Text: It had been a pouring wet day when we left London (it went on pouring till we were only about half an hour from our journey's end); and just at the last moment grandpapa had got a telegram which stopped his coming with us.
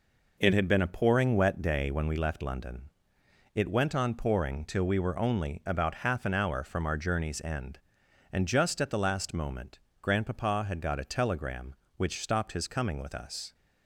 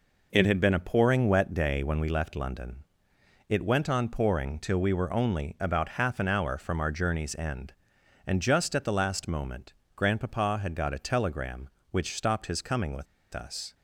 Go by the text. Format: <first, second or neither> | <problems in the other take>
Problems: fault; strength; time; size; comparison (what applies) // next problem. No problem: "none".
first | pauses between "moment" and "grandpapa"; slight; at 9.7 s; 0.24 s long; slight in the first // pauses between "with" and "us"; slight; at 13.0 s; 0.28 s long